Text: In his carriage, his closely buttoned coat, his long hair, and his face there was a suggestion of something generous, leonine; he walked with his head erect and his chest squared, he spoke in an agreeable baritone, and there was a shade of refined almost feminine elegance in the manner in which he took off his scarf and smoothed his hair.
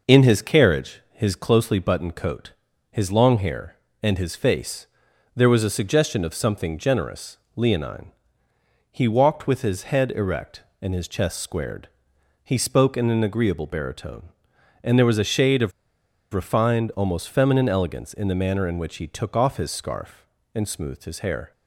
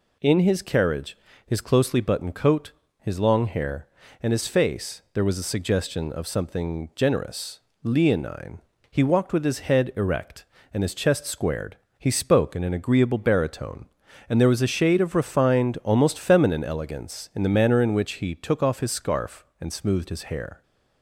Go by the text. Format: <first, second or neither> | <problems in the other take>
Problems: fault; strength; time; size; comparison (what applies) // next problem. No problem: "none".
second | pauses between "face" and "there"; noticeable; at 4.8 s; 0.48 s long // pauses between "of" and "refined"; noticeable; at 15.7 s; 0.61 s long